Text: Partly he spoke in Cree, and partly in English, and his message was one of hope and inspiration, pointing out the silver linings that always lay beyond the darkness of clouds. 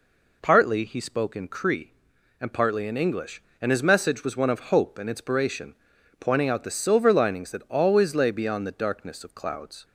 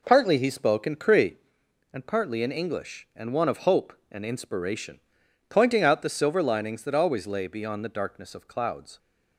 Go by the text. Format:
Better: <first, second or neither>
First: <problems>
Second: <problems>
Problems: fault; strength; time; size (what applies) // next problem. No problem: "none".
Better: first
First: none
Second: skips "his message was"; at 3.3 s